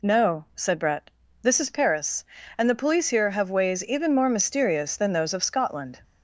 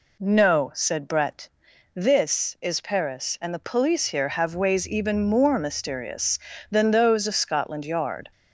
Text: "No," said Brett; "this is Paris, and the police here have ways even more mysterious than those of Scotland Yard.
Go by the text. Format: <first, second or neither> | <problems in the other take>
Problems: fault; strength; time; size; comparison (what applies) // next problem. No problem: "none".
second | stops before "Yard"; at 6.0 s